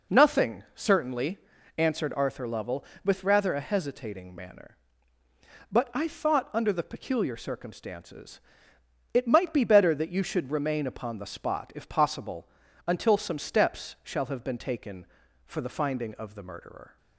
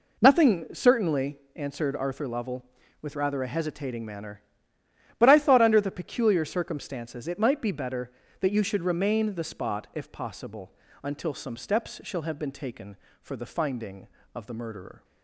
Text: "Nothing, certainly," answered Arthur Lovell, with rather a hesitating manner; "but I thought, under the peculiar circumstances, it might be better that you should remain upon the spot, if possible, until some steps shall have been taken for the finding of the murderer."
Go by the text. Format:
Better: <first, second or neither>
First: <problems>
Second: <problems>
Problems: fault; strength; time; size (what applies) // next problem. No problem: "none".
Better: first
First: none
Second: skips "upon"; at 9.3 s